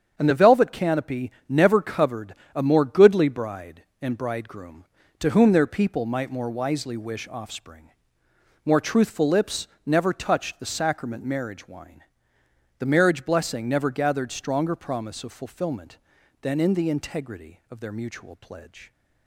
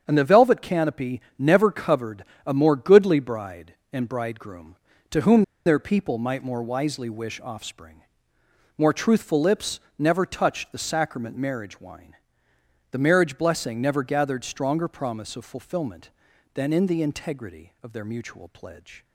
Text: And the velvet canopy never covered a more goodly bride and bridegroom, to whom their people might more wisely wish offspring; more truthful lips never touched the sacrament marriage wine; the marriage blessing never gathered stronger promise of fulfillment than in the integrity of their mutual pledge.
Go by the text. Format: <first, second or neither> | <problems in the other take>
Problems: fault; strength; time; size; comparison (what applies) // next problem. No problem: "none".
first | starts louder than the rest; strong; until 1.0 s; 7.5 dB; strong in the first // pauses between "canopy" and "never"; slight; at 1.2 s; 0.18 s long; slight in the first // pauses between "covered" and "a"; slight; at 2.2 s; 0.20 s long; slight in the first // pauses between "whom" and "their"; slight; at 5.4 s; 0.21 s long // pauses between "lips" and "never"; slight; at 9.7 s; 0.18 s long; slight in the first